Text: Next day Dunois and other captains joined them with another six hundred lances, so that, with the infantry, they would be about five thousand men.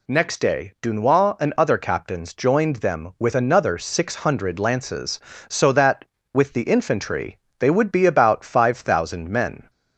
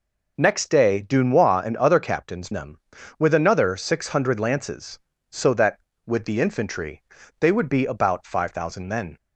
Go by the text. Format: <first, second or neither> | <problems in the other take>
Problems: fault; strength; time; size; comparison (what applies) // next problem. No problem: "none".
first | skips "joined"; at 2.5 s